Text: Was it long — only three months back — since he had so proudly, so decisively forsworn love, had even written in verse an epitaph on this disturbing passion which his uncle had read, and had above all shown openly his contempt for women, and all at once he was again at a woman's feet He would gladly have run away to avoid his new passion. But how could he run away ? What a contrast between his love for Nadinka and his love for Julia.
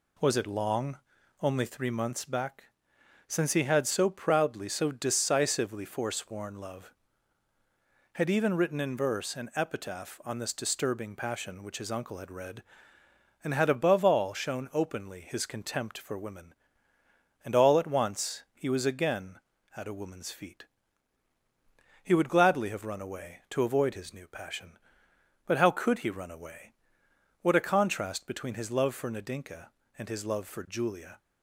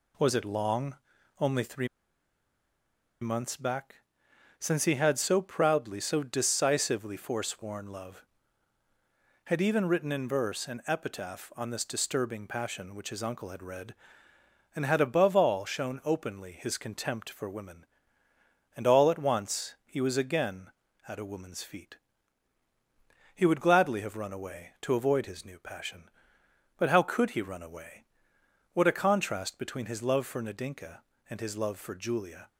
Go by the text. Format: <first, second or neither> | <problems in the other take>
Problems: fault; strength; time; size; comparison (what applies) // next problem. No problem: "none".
first | pauses between "three" and "months"; strong; at 1.8 s; 1.3 s long // pauses between "feet" and "He"; strong; at 21.9 s; 1.3 s long; strong in the first